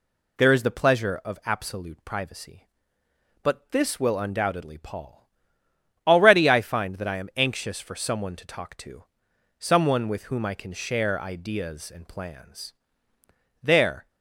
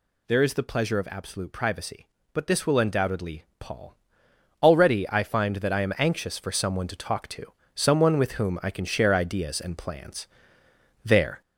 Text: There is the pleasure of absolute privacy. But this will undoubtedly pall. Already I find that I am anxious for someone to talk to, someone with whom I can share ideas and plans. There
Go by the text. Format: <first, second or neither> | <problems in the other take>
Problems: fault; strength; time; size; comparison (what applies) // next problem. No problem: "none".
first | gets louder; throughout; 3.5 dB // pauses between "undoubtedly" and "pall"; slight; at 3.4 s; 0.16 s long